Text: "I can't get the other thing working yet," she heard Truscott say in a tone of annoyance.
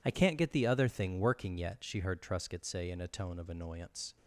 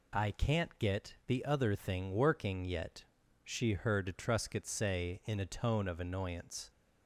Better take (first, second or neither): neither